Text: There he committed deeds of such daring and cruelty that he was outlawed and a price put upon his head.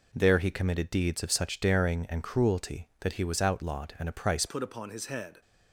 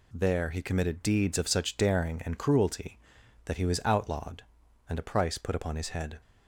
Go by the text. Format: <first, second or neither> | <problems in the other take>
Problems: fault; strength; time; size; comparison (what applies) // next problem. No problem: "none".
second | changes voice at "put"; from 4.4 s on; 1.0 s long